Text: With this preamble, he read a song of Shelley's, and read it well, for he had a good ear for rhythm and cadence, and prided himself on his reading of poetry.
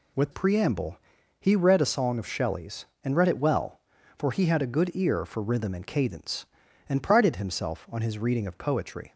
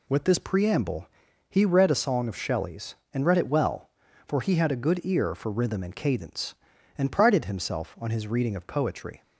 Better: second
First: skips "this"; at 0.3 s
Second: none

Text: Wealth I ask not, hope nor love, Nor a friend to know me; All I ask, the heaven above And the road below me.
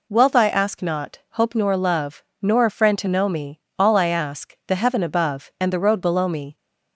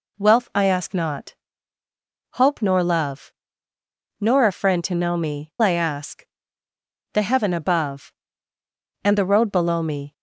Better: first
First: none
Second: skips "All"; at 5.5 s

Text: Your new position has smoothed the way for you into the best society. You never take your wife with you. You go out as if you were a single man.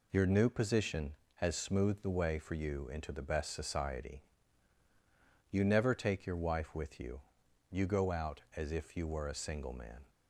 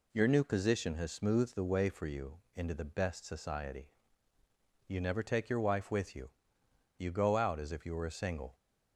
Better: first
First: none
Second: pauses between "you" and "into"; slight; at 2.4 s; 0.16 s long // stops before "man"; at 8.5 s

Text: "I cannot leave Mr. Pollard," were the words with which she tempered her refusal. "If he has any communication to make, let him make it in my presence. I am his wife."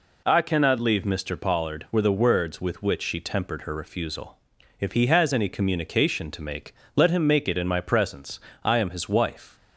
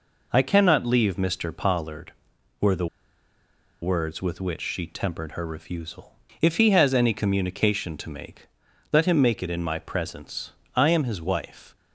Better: first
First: none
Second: pauses between "the" and "words"; noticeable; at 2.8 s; 0.95 s long

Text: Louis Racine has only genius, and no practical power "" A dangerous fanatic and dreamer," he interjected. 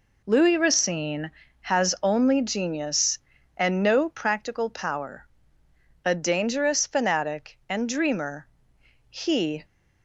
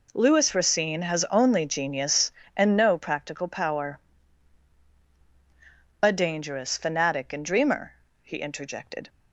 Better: second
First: stops before "interjected"; at 9.6 s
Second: none

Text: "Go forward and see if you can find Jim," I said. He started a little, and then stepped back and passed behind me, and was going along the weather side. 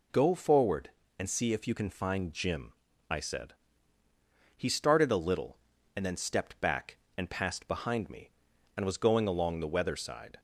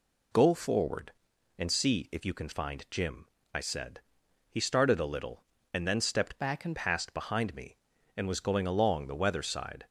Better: first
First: none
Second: changes voice from "back" to "and"; from 6.3 to 6.7 s; 0.4 s long

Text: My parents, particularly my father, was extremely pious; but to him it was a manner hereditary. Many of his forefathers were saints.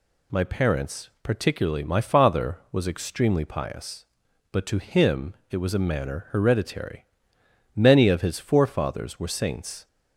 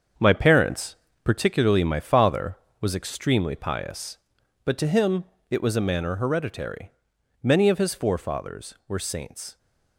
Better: first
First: pauses between "him" and "it"; slight; at 5.3 s; 0.18 s long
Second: gets quieter; strong; throughout; 7.5 dB // pauses between "him" and "it"; slight; at 5.2 s; 0.24 s long

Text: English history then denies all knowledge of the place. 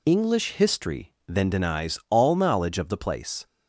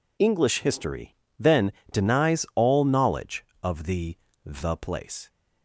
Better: first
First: pauses between "history" and "then"; slight; at 1.1 s; 0.16 s long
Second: pauses between "history" and "then"; slight; at 1.1 s; 0.24 s long // pauses between "then" and "denies"; slight; at 1.7 s; 0.20 s long // says "the" twice; at 4.4 s

